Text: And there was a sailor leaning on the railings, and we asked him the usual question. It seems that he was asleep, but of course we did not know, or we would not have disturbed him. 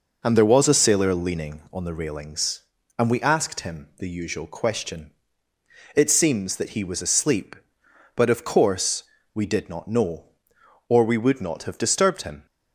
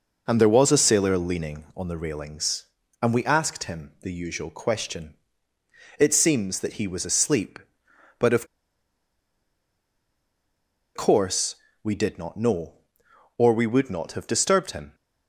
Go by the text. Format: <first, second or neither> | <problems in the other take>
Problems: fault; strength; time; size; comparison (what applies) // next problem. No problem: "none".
first | pauses between "of" and "course"; strong; at 8.4 s; 2.4 s long // pauses between "course" and "we"; slight; at 11.5 s; 0.30 s long; slight in the first